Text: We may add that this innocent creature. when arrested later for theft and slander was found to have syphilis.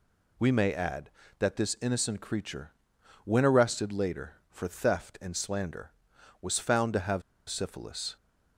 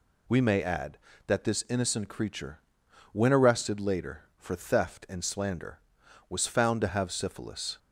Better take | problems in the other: second | pauses between "have" and "syphilis"; slight; at 7.2 s; 0.27 s long

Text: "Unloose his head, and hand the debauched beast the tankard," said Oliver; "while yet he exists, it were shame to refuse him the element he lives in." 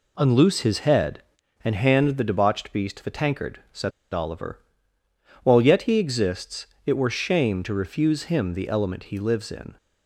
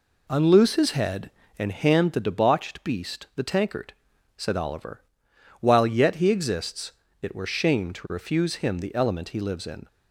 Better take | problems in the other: second | pauses between "said" and "Oliver"; slight; at 3.9 s; 0.21 s long

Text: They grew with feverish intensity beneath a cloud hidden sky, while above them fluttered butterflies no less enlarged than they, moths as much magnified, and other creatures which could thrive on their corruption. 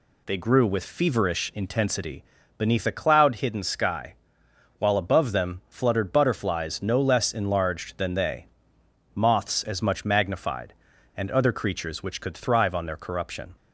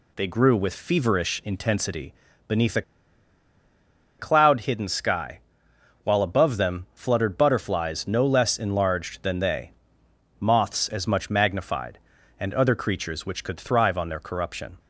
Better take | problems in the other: first | pauses between "intensity" and "beneath"; slight; at 2.1 s; 0.34 s long; slight in the first // pauses between "a" and "cloud"; strong; at 2.8 s; 1.3 s long

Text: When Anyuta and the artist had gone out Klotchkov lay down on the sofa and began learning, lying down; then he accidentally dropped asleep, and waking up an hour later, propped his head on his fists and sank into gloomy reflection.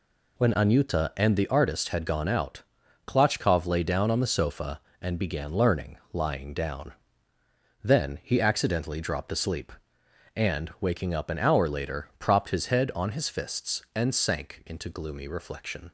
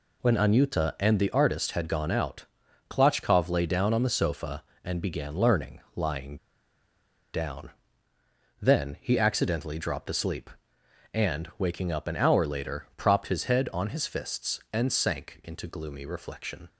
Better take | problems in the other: first | pauses between "out" and "Klotchkov"; at 2.4 s; 0.44 s long; also in the first // pauses between "lying" and "down"; noticeable; at 6.3 s; 0.98 s long

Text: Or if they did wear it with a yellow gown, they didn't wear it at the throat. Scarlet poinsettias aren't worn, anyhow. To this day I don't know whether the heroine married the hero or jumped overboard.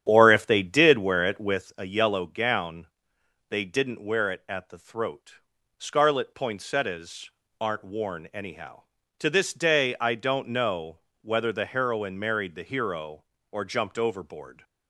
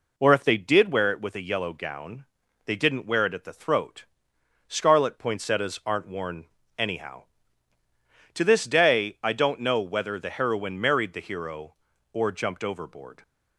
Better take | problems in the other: second | starts louder than the rest; strong; until 1.6 s; 9.5 dB // pauses between "poinsettias" and "aren't"; slight; at 7.2 s; 0.30 s long // pauses between "know" and "whether"; slight; at 10.9 s; 0.24 s long

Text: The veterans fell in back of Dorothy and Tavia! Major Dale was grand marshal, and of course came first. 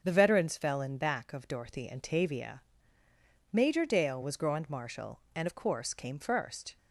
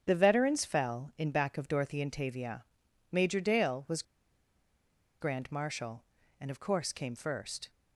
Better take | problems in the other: first | starts louder than the rest; strong; until 1.0 s; 7 dB; also in the first // pauses between "was" and "grand"; at 4.0 s; 1.1 s long

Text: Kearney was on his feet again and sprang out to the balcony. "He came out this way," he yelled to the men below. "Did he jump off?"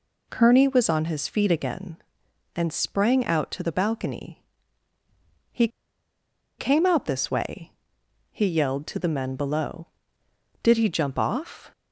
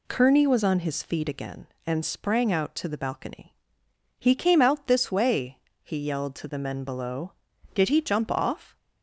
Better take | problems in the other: second | pauses between "He" and "came"; noticeable; at 5.6 s; 0.90 s long

